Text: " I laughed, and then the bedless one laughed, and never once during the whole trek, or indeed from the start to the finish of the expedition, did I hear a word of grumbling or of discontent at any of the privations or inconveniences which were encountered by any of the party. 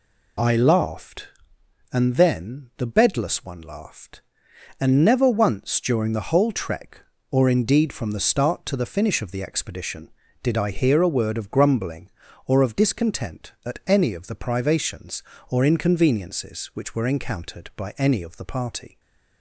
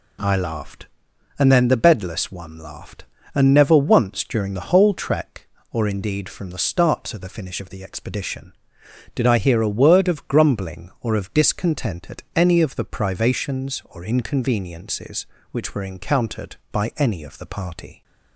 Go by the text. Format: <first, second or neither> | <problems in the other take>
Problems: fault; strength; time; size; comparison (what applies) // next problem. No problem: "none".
neither | none